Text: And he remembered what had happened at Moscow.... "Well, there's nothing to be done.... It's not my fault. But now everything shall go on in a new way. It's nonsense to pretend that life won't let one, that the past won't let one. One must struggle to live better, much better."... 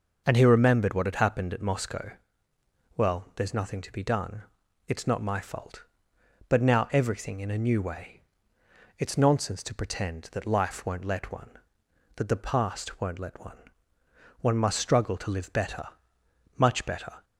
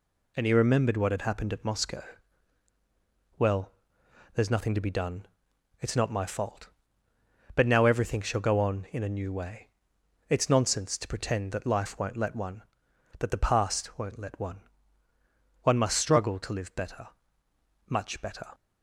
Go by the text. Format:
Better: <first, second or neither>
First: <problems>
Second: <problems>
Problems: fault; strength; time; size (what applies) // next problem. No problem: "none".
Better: second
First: skips "shall go on"; at 7.3 s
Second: none